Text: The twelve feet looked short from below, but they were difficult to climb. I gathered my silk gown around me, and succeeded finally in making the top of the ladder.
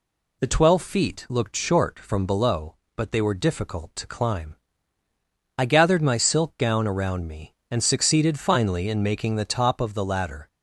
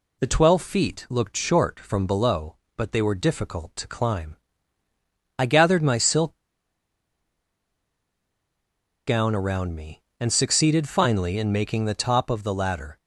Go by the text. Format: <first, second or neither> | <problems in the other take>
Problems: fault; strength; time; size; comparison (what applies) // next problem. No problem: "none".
first | pauses between "silk" and "gown"; strong; at 6.3 s; 2.6 s long